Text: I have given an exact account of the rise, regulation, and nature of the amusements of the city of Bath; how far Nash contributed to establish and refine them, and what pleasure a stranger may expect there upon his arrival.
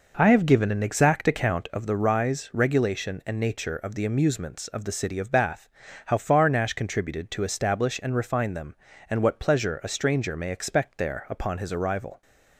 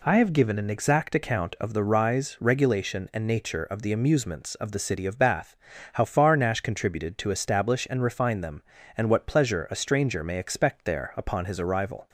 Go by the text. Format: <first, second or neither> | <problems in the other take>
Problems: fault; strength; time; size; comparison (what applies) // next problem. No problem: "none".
second | starts louder than the rest; noticeable; until 1.7 s; 5.5 dB